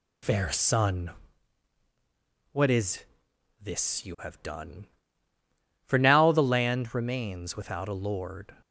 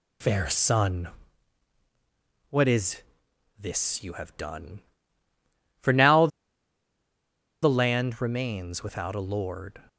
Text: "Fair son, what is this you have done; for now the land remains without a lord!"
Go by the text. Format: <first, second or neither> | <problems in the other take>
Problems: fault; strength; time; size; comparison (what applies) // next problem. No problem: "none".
first | pauses between "is" and "this"; noticeable; at 3.0 s; 0.58 s long; noticeable in the first // pauses between "now" and "the"; strong; at 6.2 s; 1.3 s long